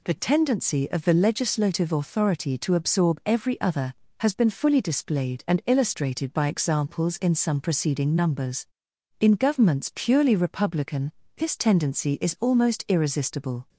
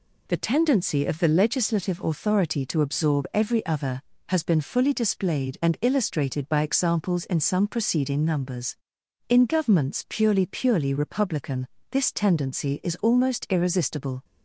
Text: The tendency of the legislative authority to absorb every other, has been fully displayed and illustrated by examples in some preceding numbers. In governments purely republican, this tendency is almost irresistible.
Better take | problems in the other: first | says "purely" twice; at 10.4 s

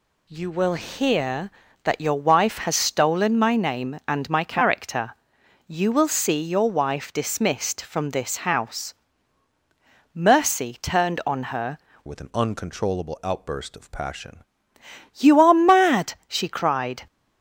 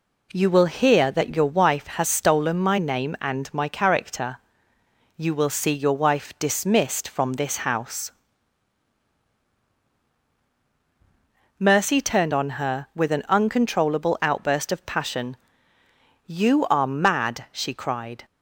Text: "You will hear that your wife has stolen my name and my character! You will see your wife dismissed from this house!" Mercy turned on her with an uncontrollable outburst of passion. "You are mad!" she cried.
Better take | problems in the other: second | changes voice from "with" to "passion"; from 12.0 to 14.3 s; 2.3 s long

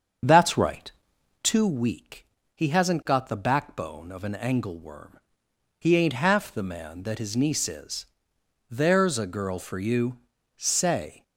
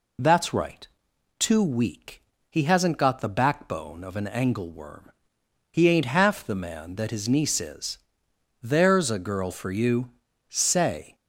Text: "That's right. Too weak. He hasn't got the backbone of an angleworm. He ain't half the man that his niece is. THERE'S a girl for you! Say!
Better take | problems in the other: second | starts louder than the rest; strong; until 1.5 s; 7 dB

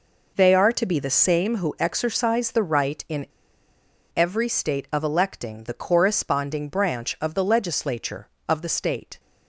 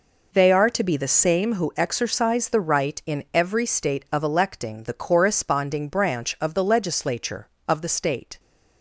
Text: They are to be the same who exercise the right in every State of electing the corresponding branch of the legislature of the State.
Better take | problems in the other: second | pauses between "in" and "every"; noticeable; at 3.2 s; 0.88 s long

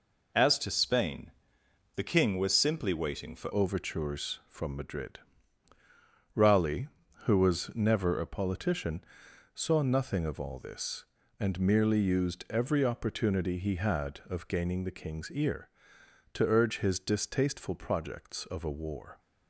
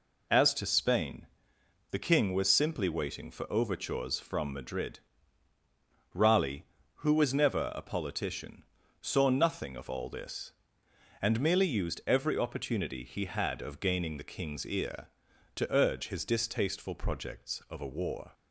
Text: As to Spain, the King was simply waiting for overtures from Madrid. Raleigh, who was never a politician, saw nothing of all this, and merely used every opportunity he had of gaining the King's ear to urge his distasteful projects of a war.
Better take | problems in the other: second | changes voice at "overtures"; from 3.5 s on; 15.6 s long

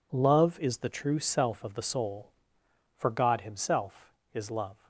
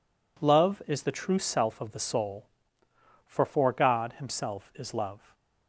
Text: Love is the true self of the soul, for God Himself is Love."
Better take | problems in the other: first | says "for" twice; at 3.4 s

